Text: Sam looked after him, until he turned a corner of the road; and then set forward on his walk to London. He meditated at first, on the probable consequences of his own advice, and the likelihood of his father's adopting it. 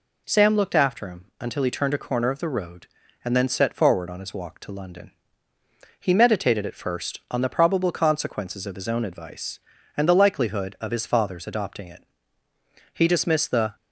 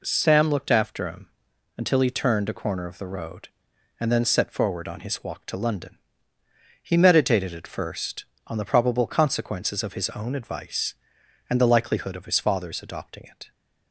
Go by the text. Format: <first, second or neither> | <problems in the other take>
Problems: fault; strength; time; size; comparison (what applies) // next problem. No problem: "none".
second | goes on to say "He dismissed the"; noticeable; from 12.9 s on; 0.82 s long